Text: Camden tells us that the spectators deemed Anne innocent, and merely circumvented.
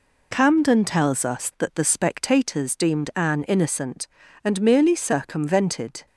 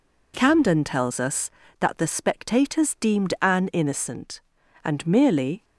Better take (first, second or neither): first